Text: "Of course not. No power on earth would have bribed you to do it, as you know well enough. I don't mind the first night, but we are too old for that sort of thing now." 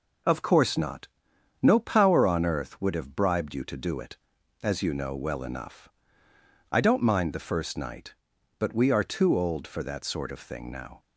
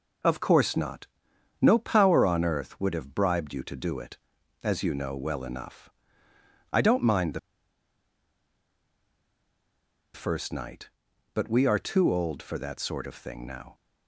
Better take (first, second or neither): first